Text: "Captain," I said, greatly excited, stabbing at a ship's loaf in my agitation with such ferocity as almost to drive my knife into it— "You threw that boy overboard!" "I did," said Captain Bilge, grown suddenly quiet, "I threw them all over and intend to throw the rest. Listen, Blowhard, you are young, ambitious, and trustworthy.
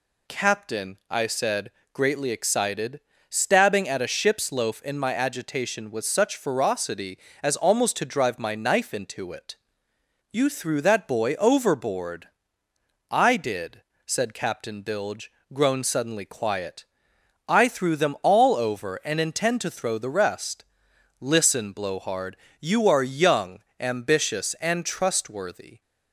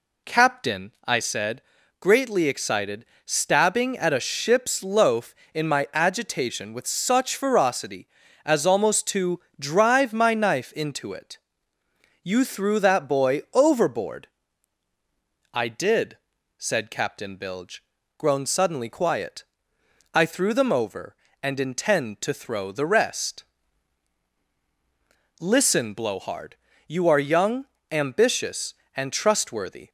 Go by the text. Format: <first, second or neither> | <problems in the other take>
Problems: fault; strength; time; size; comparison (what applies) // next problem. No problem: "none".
first | pauses between "to" and "drive"; slight; at 9.3 s; 0.20 s long // skips "all"; at 20.7 s